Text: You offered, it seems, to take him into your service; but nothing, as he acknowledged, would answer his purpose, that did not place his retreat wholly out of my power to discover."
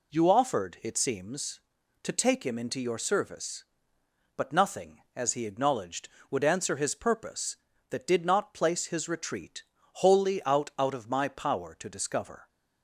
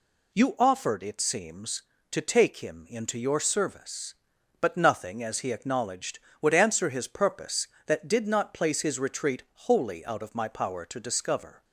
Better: second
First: pauses between "retreat" and "wholly"; at 9.6 s; 0.40 s long // says "out" twice; at 10.7 s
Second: pauses between "retreat" and "wholly"; slight; at 9.4 s; 0.24 s long

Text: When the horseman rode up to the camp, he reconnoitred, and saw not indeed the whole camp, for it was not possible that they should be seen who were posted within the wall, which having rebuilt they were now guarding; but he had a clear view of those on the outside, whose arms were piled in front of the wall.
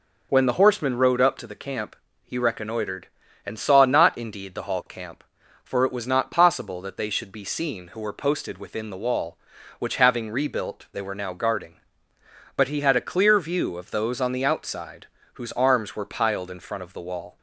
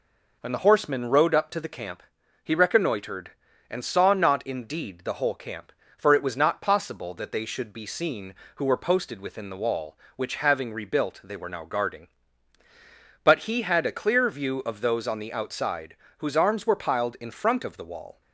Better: second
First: says "hall" for "whole"; at 4.6 s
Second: none

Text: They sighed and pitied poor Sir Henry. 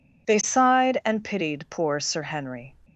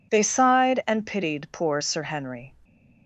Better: neither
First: none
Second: none

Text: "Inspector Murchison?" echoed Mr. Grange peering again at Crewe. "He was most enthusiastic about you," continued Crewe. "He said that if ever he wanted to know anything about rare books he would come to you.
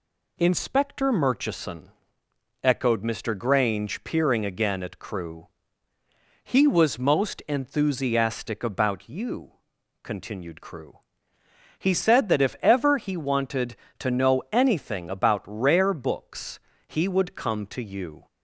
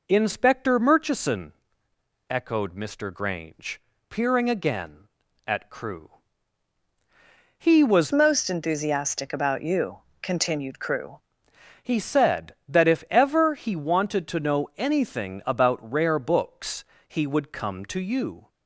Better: first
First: pauses between "books" and "he"; slight; at 16.5 s; 0.28 s long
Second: pauses between "Grange" and "peering"; slight; at 3.7 s; 0.28 s long // changes voice from "most" to "Crewe"; from 8.1 to 11.1 s; 3.0 s long // pauses between "books" and "he"; slight; at 16.8 s; 0.24 s long

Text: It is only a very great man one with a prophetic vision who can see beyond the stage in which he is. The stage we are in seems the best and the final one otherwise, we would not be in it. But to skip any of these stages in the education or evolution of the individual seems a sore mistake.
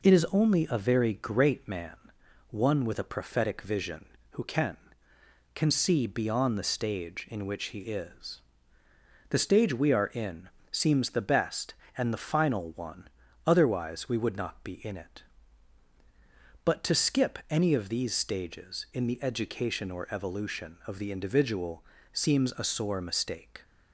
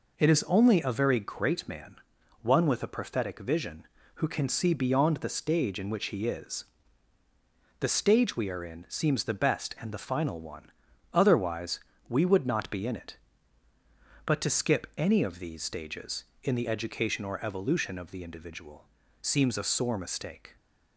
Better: second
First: pauses between "man" and "one"; noticeable; at 1.9 s; 0.54 s long // says "can" twice; at 5.5 s // pauses between "in" and "seems"; slight; at 10.4 s; 0.22 s long // pauses between "one" and "otherwise"; slight; at 13.0 s; 0.36 s long // pauses between "individual" and "seems"; slight; at 21.8 s; 0.30 s long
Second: pauses between "man" and "one"; at 1.9 s; 0.44 s long // pauses between "one" and "otherwise"; at 10.7 s; 0.42 s long // pauses between "individual" and "seems"; at 18.8 s; 0.38 s long

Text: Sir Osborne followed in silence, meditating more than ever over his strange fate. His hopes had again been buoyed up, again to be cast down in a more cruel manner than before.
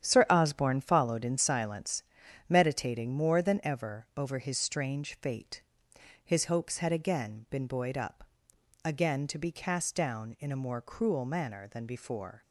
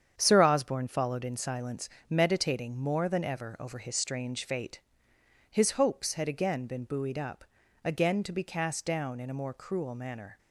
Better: first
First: starts louder than the rest; strong; until 1.0 s; 9.5 dB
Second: starts louder than the rest; strong; until 1.1 s; 8 dB // stops before "than before"; at 10.3 s

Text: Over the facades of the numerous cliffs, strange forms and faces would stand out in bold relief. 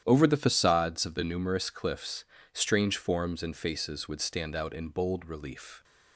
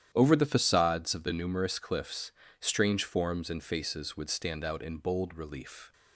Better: neither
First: starts louder than the rest; strong; until 1.0 s; 10.5 dB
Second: starts louder than the rest; strong; until 1.1 s; 10.5 dB

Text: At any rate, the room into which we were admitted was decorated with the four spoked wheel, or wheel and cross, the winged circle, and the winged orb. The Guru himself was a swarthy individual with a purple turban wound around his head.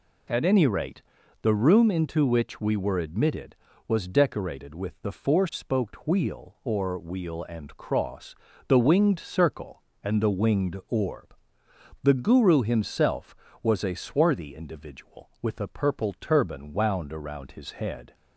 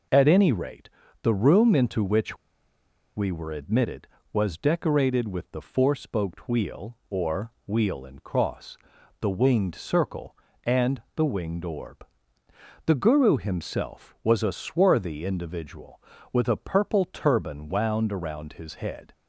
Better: first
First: none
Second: pauses between "which" and "we"; noticeable; at 2.3 s; 0.80 s long

